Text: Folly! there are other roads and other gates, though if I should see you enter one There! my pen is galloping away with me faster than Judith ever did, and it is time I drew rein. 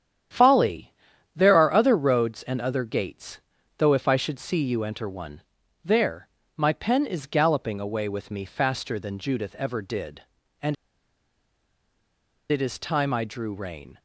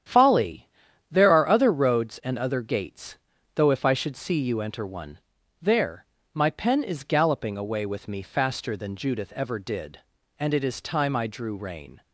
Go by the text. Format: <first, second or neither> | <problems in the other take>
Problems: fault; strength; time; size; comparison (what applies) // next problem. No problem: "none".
second | starts louder than the rest; strong; until 1.7 s; 9.5 dB; strong in the second // pauses between "one" and "There"; at 5.4 s; 0.42 s long; also in the second // pauses between "and" and "it"; strong; at 10.7 s; 1.7 s long